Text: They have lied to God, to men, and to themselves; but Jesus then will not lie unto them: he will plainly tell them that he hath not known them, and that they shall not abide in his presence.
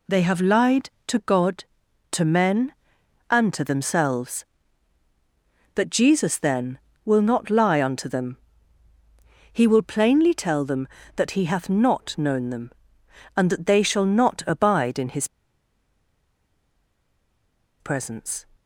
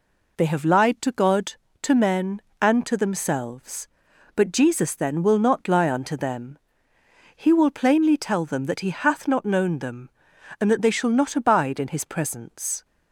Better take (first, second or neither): second